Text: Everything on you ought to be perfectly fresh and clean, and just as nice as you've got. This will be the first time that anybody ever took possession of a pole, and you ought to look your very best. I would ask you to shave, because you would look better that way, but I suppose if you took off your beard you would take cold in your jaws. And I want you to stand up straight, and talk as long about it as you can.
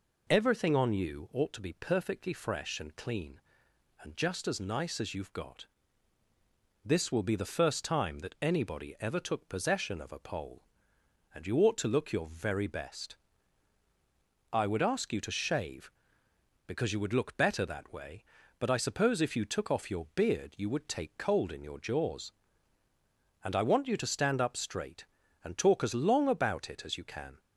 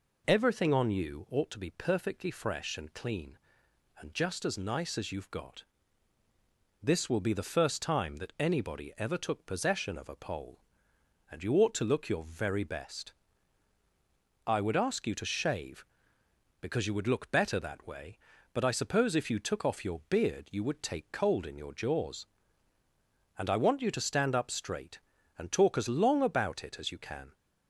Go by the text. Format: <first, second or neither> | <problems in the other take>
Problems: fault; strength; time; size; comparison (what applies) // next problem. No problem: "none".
neither | none